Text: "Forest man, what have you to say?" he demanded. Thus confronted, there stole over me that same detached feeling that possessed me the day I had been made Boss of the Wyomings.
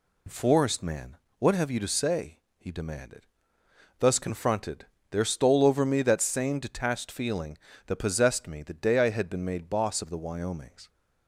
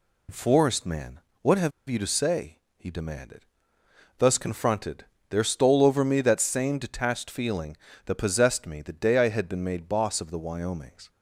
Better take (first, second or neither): first